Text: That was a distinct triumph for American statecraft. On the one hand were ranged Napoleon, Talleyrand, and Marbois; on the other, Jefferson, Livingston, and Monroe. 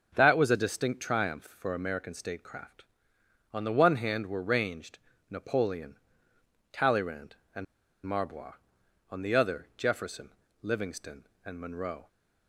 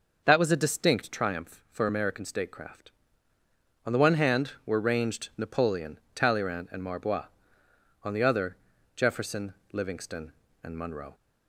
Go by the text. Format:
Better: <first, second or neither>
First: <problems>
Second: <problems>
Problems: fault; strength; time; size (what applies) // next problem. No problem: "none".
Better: second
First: starts louder than the rest; until 1.1 s; 7 dB // pauses between "ranged" and "Napoleon"; slight; at 4.9 s; 0.32 s long // pauses between "and" and "Marbois"; at 7.6 s; 0.40 s long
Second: none